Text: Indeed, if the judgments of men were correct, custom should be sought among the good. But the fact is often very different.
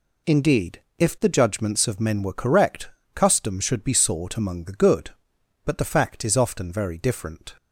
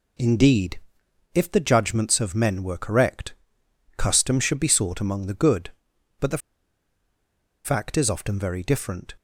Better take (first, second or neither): first